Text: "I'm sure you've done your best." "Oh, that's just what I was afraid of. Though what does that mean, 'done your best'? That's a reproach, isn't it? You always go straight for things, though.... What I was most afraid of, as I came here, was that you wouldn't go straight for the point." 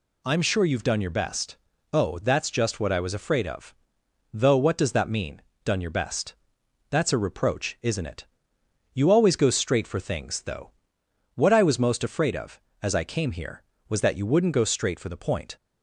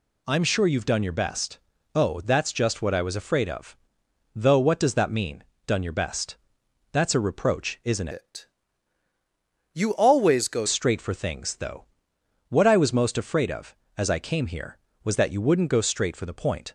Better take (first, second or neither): first